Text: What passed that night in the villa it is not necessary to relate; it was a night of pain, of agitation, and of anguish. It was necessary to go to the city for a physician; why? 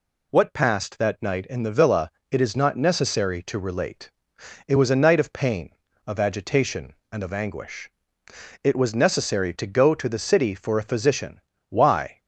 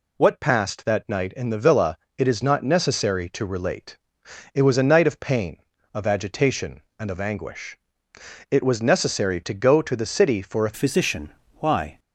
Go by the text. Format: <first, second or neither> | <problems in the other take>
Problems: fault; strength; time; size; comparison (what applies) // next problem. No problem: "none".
first | pauses between "villa" and "it"; slight; at 1.9 s; 0.18 s long; slight in the first // changes voice at "physician"; from 10.7 s on; 1.2 s long